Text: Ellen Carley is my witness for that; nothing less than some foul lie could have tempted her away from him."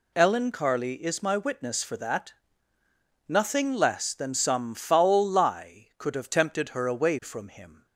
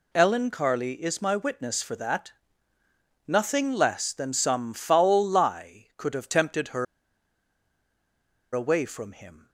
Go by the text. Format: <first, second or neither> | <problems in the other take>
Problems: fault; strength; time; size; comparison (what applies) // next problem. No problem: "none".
first | pauses between "her" and "away"; strong; at 6.8 s; 1.7 s long